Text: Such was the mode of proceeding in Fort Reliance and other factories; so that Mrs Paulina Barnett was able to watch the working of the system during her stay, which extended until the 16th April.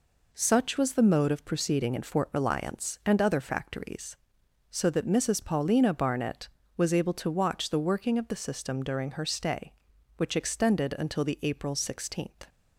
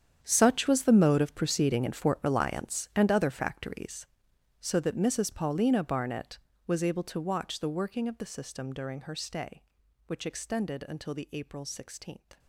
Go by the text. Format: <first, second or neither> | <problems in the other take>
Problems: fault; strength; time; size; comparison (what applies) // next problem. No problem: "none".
first | gets quieter; strong; throughout; 14.5 dB